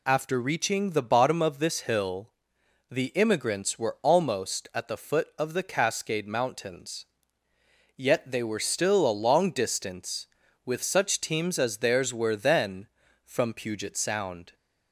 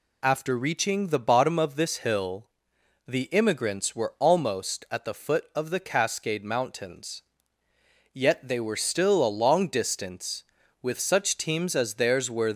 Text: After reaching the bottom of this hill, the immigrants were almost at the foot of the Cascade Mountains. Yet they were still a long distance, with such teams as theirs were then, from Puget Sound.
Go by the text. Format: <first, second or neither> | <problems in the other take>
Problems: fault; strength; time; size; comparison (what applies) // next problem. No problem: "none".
first | stops before "then from Puget Sound"; at 12.5 s